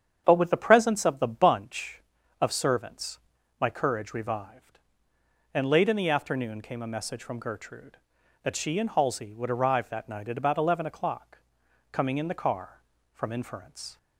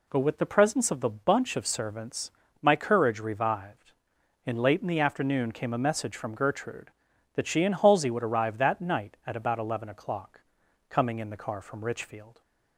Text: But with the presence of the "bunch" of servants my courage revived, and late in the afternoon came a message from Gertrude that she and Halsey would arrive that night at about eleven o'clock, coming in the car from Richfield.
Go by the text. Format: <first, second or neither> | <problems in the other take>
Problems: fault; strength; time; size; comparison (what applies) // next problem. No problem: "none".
second | starts louder than the rest; strong; until 1.2 s; 8.5 dB // pauses between "servants" and "my"; at 3.1 s; 0.42 s long; slight in the second // says "Inference" for "Richfield"; at 13.3 s